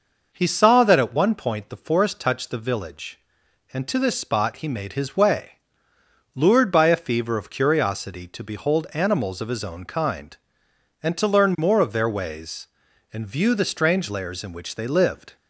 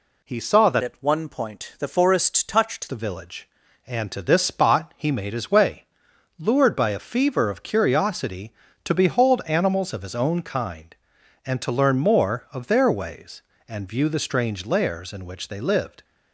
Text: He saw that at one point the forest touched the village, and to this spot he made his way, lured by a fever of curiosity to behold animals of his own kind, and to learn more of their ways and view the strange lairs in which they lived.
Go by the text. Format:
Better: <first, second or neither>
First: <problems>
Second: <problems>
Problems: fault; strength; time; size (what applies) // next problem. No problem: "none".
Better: first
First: none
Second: changes voice from "at" to "touched"; from 0.8 to 2.8 s; 2.0 s long